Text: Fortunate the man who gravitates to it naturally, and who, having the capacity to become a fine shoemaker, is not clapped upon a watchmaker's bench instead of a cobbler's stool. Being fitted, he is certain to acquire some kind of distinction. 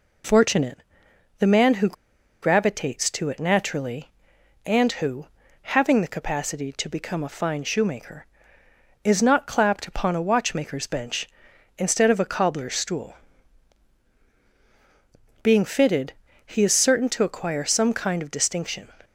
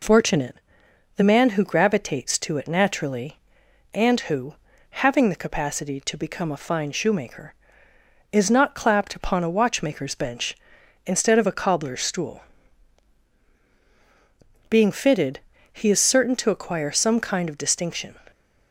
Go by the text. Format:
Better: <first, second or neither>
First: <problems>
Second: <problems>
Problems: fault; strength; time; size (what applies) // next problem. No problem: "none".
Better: second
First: pauses between "Fortunate" and "the"; noticeable; at 0.7 s; 0.58 s long // pauses between "who" and "gravitates"; noticeable; at 1.9 s; 0.47 s long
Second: pauses between "Fortunate" and "the"; noticeable; at 0.5 s; 0.58 s long